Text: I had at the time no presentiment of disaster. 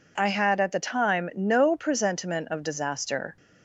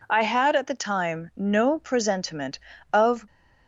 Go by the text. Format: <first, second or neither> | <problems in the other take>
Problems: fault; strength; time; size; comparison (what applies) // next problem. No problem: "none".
first | stops before "disaster"; at 3.2 s